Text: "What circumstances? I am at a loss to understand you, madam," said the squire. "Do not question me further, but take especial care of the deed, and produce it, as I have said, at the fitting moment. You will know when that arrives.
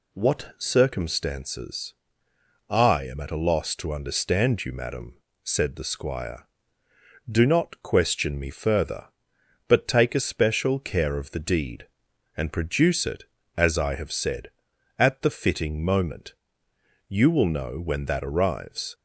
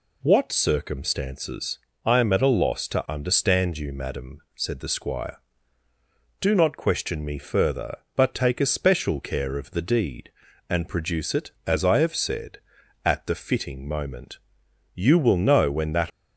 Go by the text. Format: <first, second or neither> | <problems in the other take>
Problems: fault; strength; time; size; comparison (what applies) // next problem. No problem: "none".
first | stops before "arrives"; at 16.1 s